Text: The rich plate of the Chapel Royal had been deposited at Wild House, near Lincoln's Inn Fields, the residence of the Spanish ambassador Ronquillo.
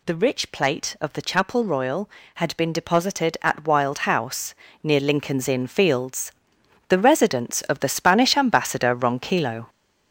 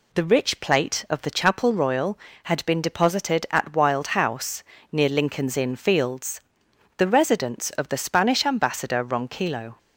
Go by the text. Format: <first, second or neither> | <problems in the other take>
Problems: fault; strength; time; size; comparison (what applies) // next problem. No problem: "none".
second | gets louder; noticeable; throughout; 5 dB